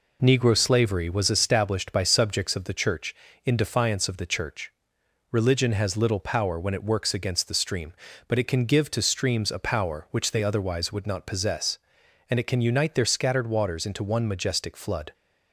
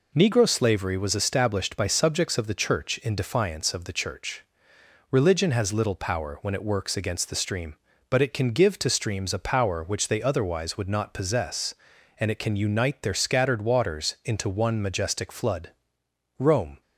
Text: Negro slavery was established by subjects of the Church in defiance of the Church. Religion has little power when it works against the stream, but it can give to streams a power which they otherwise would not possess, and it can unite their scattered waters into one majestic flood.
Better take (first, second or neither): first